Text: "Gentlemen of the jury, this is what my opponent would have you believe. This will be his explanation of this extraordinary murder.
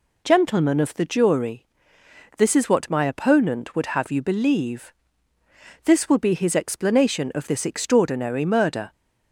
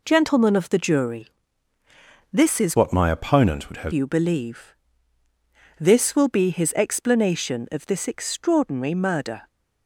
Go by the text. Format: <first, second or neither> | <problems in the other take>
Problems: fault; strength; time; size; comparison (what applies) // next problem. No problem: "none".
first | changes voice from "what" to "have"; from 2.7 to 3.9 s; 1.2 s long